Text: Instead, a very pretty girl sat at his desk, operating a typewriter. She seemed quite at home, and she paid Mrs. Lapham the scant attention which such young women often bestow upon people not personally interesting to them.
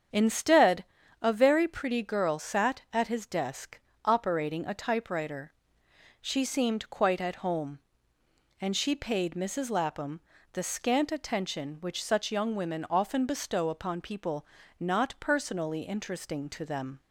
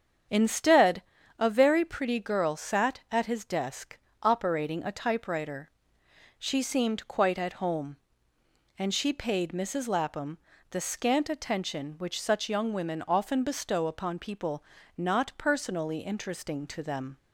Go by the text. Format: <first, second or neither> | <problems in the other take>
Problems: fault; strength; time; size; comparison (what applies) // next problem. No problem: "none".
neither | starts louder than the rest; strong; the same in both // pauses between "Lapham" and "the"; slight; the same in both // pauses between "people" and "not"; slight; the same in both